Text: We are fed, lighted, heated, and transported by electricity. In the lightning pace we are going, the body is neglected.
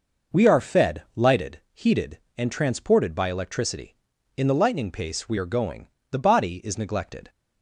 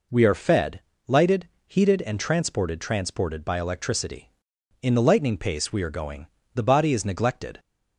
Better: first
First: none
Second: says "transported" twice; at 2.8 s

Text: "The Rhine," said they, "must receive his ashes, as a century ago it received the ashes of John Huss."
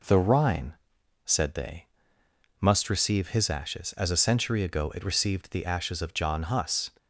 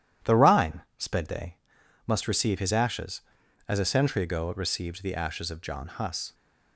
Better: first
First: none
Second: says "sped" for "said"; at 0.9 s

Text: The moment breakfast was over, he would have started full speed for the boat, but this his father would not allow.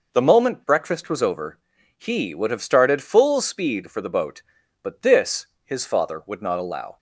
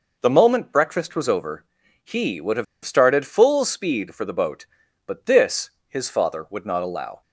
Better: first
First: pauses between "this" and "his"; slight; at 5.4 s; 0.18 s long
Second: pauses between "have" and "started"; slight; at 2.6 s; 0.20 s long // pauses between "this" and "his"; slight; at 5.6 s; 0.18 s long

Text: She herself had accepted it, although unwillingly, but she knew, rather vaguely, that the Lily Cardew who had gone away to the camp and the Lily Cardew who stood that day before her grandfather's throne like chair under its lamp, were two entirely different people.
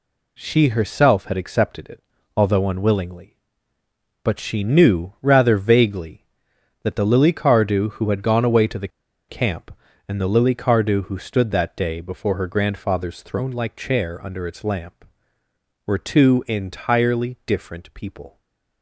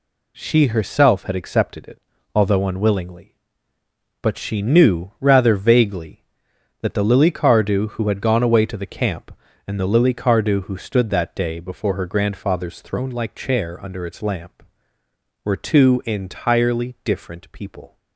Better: second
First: pauses between "the" and "camp"; at 8.8 s; 0.40 s long // stays silent after the last word; slight; from 18.3 s on; 0.5 s long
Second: none

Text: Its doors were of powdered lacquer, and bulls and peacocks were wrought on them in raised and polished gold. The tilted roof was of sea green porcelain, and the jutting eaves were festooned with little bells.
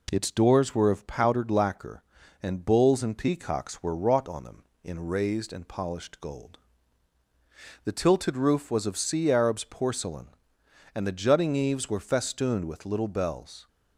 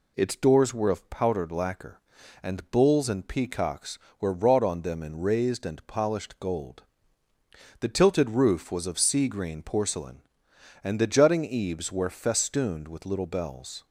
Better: second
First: says "arabs" for "green"; at 9.3 s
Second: none

